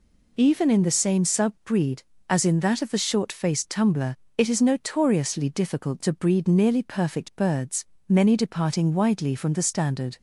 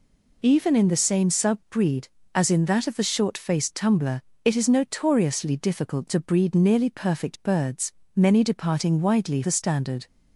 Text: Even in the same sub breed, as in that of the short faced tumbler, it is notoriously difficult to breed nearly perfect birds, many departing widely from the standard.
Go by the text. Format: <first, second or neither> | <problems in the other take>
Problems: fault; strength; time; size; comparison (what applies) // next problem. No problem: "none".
first | skips "from"; at 9.4 s